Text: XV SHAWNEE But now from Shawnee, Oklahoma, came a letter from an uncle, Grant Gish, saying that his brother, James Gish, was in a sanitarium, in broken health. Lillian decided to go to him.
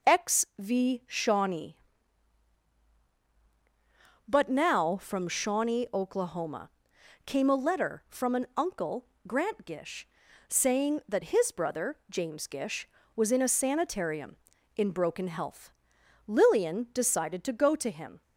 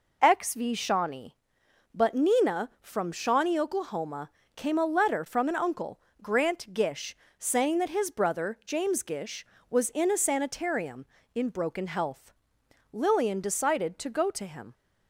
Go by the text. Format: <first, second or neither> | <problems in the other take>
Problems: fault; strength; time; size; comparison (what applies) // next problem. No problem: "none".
first | says "nina" for "now"; at 2.1 s